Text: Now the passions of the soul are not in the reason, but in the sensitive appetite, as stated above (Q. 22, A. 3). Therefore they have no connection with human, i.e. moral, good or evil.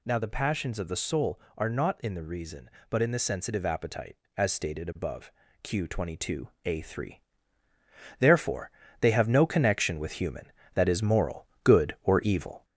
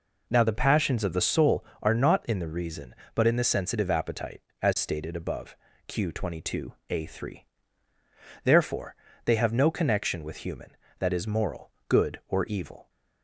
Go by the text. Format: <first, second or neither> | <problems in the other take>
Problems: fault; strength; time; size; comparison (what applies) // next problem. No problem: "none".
second | gets louder; slight; throughout; 2.5 dB // pauses between "Therefore" and "they"; slight; at 8.7 s; 0.30 s long; slight in the second